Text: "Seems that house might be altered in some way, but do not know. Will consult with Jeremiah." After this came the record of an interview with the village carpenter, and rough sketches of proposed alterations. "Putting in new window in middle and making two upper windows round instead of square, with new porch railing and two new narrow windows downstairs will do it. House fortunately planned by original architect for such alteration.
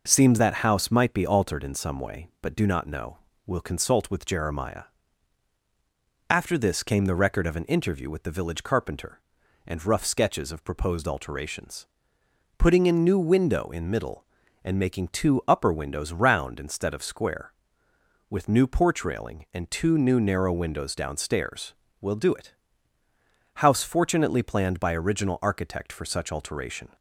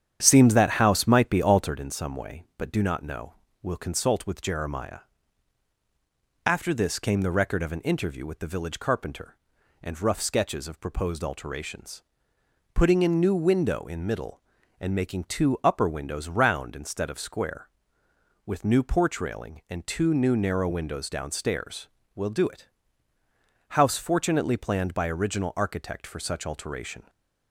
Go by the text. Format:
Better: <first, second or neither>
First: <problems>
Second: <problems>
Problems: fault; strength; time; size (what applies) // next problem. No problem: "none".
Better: first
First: none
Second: starts louder than the rest; strong; until 1.8 s; 9 dB